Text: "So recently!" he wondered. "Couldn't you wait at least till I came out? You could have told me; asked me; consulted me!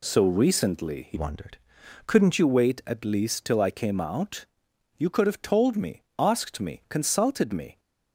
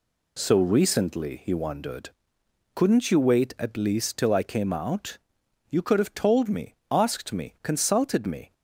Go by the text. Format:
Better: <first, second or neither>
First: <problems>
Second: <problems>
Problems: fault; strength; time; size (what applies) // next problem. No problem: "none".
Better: second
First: changes voice from "wondered" to "Couldn't"; from 1.1 to 2.3 s; 1.2 s long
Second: none